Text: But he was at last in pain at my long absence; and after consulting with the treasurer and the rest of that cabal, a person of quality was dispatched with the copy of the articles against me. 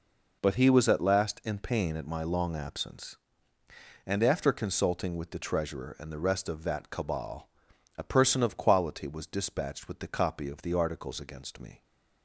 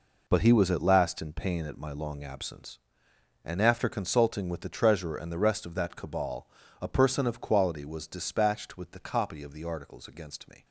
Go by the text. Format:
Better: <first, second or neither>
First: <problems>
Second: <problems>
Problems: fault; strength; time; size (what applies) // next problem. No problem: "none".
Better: neither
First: none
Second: none